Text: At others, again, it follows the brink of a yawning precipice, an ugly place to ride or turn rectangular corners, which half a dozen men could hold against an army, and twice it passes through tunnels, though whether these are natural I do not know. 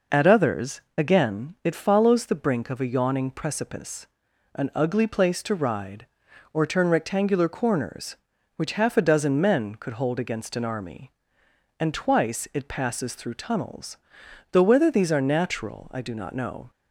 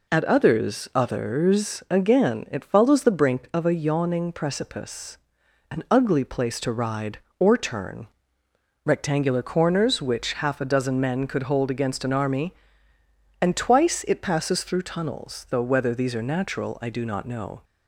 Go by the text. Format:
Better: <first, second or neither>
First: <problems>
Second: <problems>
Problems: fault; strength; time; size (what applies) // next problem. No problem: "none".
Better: first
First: none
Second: says "others" twice; at 0.9 s // pauses between "turn" and "rectangular"; noticeable; at 8.0 s; 0.78 s long